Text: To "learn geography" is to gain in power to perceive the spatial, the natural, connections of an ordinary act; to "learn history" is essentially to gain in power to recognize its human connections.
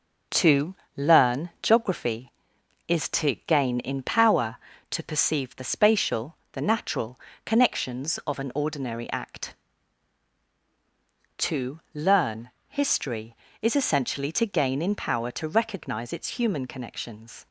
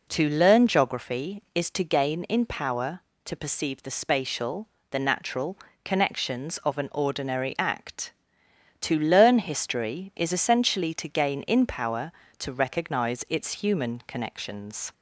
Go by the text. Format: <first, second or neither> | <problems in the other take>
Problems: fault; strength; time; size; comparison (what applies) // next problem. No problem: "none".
second | gets quieter; noticeable; throughout; 5.5 dB // pauses between "To" and "learn"; slight; at 0.7 s; 0.20 s long // pauses between "to" and "learn"; slight; at 11.7 s; 0.16 s long // pauses between "learn" and "history"; slight; at 12.5 s; 0.16 s long